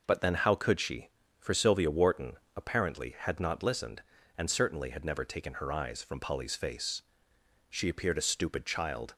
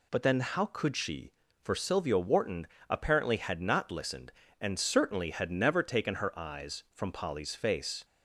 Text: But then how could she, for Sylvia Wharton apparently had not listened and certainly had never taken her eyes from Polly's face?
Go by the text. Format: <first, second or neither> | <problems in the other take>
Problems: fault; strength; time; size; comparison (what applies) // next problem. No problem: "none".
second | pauses between "Wharton" and "apparently"; slight; at 2.3 s; 0.20 s long; slight in the second // goes on to say "She appeared a stupid child"; from 7.6 s on; 1.4 s long